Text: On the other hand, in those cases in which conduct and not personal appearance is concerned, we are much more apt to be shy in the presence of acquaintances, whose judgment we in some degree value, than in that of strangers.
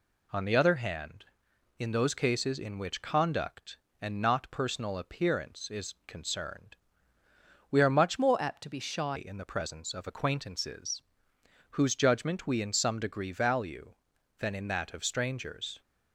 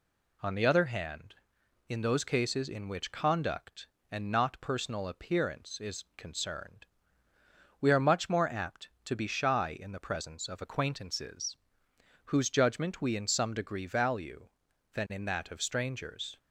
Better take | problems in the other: second | changes voice from "more" to "shy"; from 8.1 to 9.1 s; 1.0 s long

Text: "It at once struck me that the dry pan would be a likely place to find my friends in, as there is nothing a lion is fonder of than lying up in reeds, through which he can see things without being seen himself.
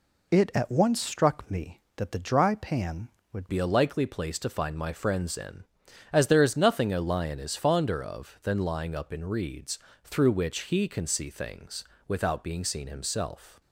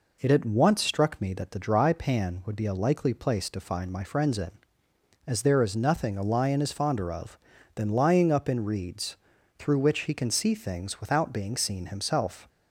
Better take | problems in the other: second | changes voice at "be"; from 3.4 s on; 10.2 s long // pauses between "things" and "without"; slight; at 11.8 s; 0.24 s long

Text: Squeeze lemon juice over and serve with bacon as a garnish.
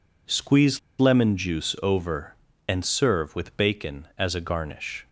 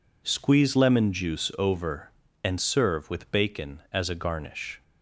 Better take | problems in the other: second | pauses between "Squeeze" and "lemon"; slight; at 0.7 s; 0.20 s long

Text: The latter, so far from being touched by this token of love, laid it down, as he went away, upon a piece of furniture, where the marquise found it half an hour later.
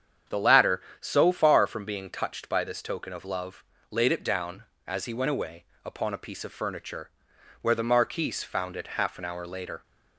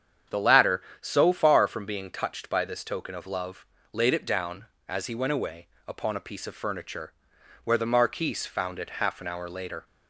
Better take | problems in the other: neither | starts louder than the rest; strong; the same in both

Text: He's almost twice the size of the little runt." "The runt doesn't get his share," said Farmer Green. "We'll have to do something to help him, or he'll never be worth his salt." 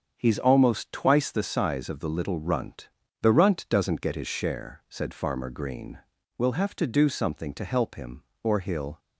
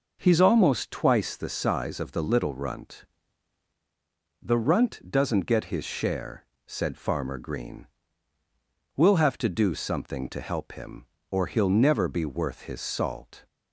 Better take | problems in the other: second | starts louder than the rest; strong; until 1.1 s; 7.5 dB // stops before "never be worth his salt"; at 8.9 s

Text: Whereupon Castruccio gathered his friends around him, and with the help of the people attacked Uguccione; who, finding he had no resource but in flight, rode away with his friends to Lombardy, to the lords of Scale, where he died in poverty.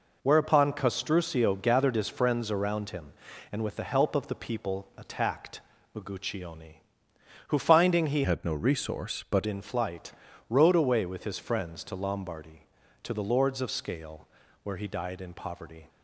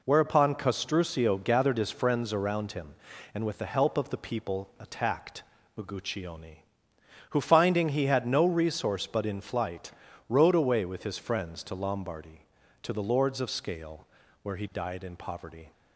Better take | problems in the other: second | pauses between "attacked" and "Uguccione"; slight; at 5.5 s; 0.36 s long; slight in the second // changes voice from "had" to "but"; from 8.2 to 9.4 s; 1.2 s long

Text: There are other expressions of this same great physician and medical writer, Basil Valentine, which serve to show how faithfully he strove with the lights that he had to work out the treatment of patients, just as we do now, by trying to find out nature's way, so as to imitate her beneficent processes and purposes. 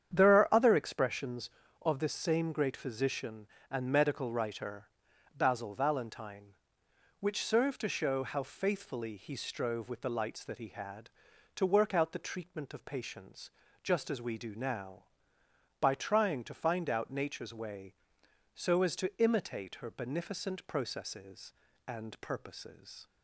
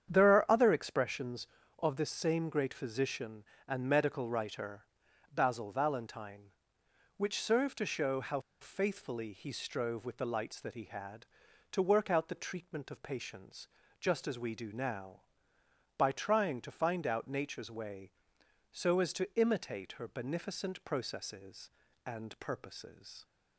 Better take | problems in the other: first | starts louder than the rest; strong; until 1.1 s; 8.5 dB; strong in the first // pauses between "how" and "faithfully"; slight; at 8.3 s; 0.21 s long

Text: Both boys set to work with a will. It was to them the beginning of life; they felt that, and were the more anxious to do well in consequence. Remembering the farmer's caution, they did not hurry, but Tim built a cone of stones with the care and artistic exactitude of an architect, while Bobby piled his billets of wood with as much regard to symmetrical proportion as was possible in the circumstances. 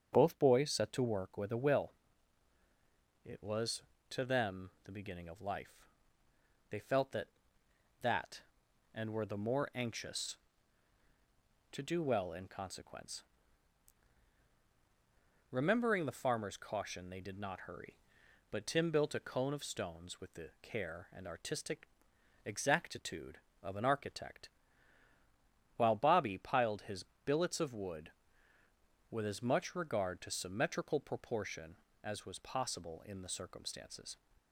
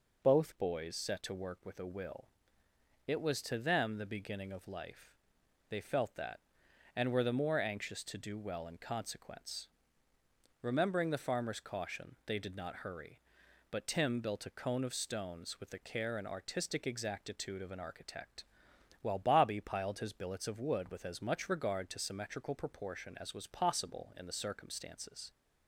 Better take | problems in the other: second | starts louder than the rest; strong; until 1.1 s; 7.5 dB // says "that" twice; at 8.0 s // pauses between "artistic" and "exactitude"; noticeable; at 21.8 s; 0.58 s long // pauses between "his" and "billets"; slight; at 27.0 s; 0.22 s long

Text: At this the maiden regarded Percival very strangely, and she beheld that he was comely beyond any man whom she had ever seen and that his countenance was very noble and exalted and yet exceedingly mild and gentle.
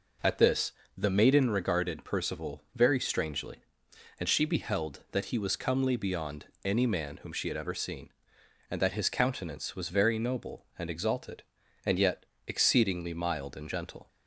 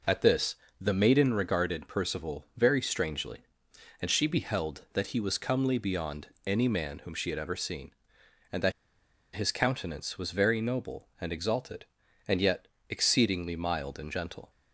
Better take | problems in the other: first | pauses between "this" and "the"; slight; at 0.5 s; 0.26 s long; slight in the first // pauses between "beyond" and "any"; slight; at 6.2 s; 0.18 s long; slight in the first // pauses between "that" and "his"; noticeable; at 8.7 s; 0.63 s long // pauses between "yet" and "exceedingly"; slight; at 12.6 s; 0.24 s long; slight in the first

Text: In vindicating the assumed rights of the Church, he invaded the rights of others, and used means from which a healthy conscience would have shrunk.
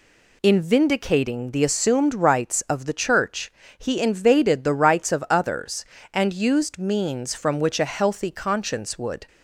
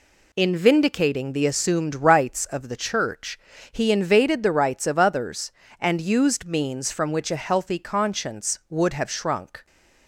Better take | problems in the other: second | stops before "have shrunk"; at 9.2 s

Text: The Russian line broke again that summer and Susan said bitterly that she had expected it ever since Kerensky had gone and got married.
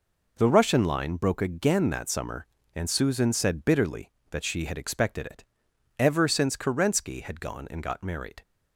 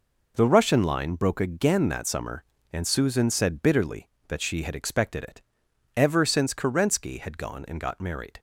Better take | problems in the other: neither | pauses between "it" and "ever"; noticeable; the same in both

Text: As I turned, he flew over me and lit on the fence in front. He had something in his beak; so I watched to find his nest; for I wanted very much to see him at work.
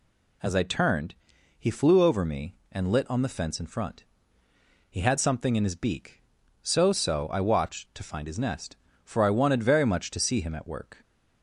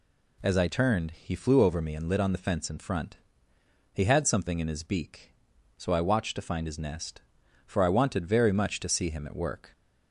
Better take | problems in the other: second | says "so" twice; at 6.9 s

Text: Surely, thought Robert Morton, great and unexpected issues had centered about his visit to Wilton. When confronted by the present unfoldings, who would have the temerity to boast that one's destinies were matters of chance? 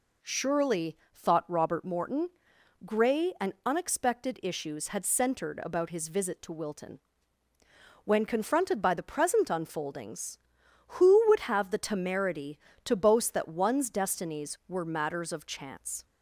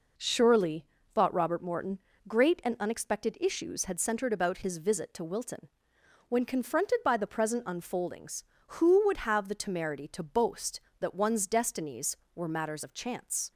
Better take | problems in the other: second | says "grey" for "great"; at 2.8 s

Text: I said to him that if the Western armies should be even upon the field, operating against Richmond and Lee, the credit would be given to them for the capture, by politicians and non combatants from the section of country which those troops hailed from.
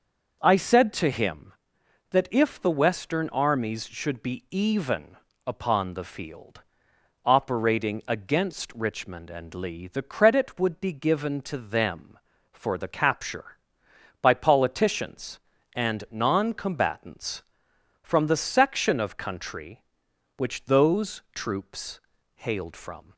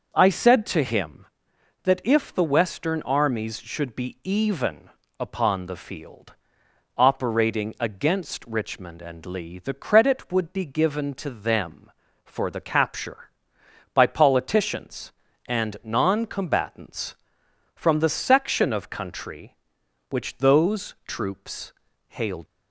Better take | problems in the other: first | starts louder than the rest; until 1.1 s; 6 dB; also in the first // pauses between "even" and "upon"; slight; at 4.8 s; 0.28 s long; slight in the first // pauses between "troops" and "hailed"; slight; at 21.7 s; 0.36 s long; slight in the first // stops before "from"; at 22.4 s

